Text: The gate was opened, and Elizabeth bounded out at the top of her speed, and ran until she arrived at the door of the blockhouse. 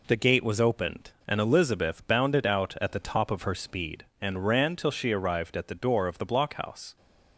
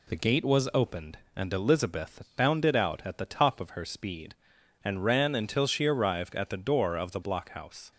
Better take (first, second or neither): second